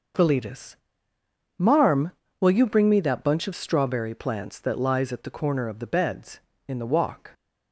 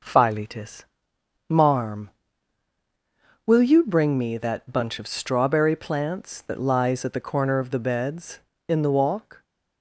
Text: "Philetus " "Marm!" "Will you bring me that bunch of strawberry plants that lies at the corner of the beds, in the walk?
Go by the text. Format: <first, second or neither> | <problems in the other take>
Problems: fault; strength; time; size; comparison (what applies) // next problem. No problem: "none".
neither | none